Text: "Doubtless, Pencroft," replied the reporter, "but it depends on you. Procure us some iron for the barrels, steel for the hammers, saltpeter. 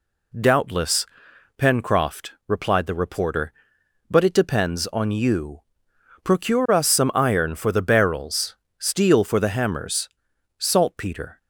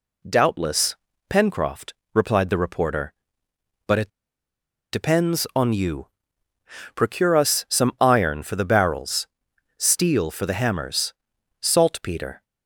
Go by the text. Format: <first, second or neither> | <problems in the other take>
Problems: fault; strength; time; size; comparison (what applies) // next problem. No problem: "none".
first | pauses between "it" and "depends"; noticeable; at 4.0 s; 0.82 s long